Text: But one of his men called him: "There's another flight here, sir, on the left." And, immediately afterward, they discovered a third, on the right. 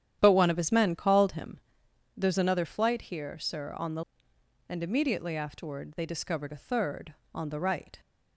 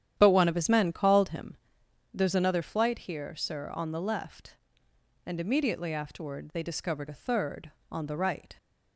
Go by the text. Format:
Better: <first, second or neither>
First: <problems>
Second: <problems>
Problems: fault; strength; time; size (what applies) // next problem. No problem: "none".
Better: second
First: starts louder than the rest; strong; until 1.2 s; 10 dB // skips "left"; at 4.3 s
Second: starts louder than the rest; strong; until 1.1 s; 10 dB